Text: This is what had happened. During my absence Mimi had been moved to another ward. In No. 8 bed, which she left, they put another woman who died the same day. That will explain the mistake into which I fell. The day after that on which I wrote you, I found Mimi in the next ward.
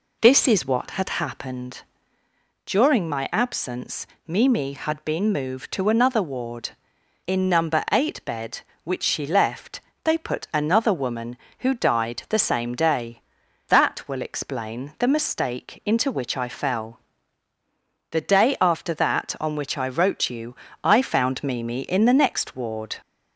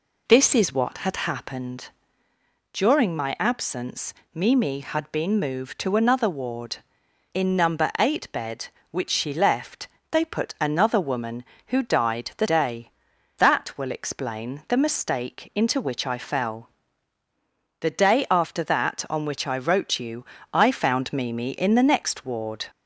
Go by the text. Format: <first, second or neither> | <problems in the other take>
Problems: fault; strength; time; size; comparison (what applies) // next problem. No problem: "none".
first | pauses between "absence" and "Mimi"; slight; at 4.1 s; 0.22 s long; slight in the first // skips "same"; at 12.4 s